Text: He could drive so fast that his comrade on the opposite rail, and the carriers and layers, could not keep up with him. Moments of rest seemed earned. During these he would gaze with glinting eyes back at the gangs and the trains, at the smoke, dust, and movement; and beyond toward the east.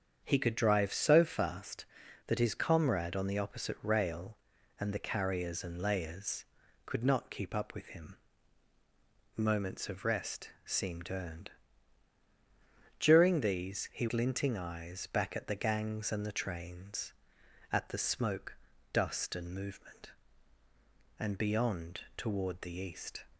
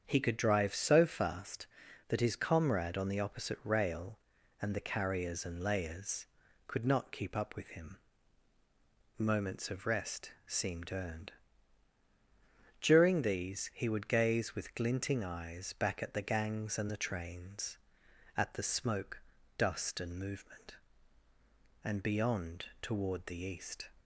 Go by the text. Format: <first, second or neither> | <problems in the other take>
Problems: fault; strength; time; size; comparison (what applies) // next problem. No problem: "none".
second | starts louder than the rest; strong; until 1.2 s; 7.5 dB; strong in the second // pauses between "rest" and "seemed"; slight; at 10.4 s; 0.16 s long; slight in the second // skips "would gaze with"; at 14.0 s // pauses between "beyond" and "toward"; slight; at 22.0 s; 0.16 s long; slight in the second